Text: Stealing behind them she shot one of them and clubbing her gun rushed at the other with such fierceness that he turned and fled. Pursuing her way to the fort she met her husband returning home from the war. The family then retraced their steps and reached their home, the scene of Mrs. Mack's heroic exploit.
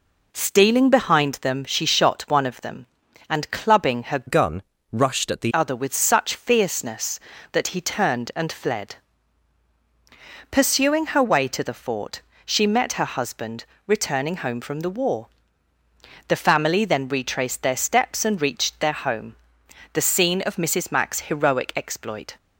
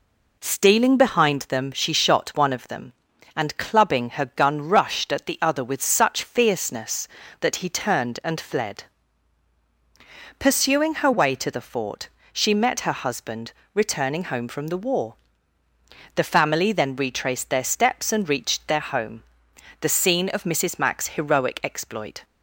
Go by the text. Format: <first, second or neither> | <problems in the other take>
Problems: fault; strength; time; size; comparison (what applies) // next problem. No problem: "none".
second | changes voice from "gun" to "the"; from 4.2 to 5.5 s; 1.3 s long // pauses between "gun" and "rushed"; slight; at 4.6 s; 0.30 s long // pauses between "fort" and "she"; slight; at 12.2 s; 0.24 s long; slight in the second // pauses between "husband" and "returning"; slight; at 13.6 s; 0.22 s long; slight in the second